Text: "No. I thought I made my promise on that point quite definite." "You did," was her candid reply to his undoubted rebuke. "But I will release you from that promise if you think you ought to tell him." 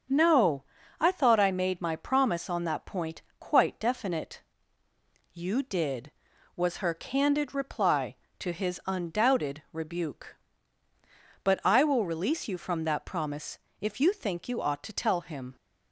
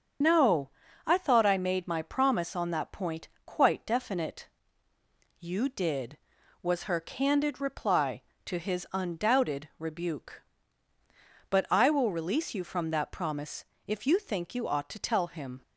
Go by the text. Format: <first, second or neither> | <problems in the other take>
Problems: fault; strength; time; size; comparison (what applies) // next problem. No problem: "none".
first | loses the start of "No"; at 0.2 s; 50 ms // starts louder than the rest; until 1.5 s; 7 dB; strong in the first // pauses between "point" and "quite"; slight; at 3.2 s; 0.18 s long; slight in the first // pauses between "promise" and "if"; slight; at 13.6 s; 0.20 s long; slight in the first